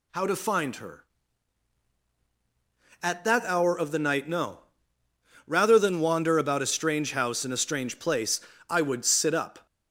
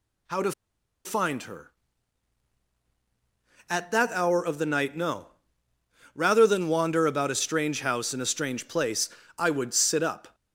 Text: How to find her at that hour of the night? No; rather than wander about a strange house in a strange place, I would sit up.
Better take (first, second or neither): first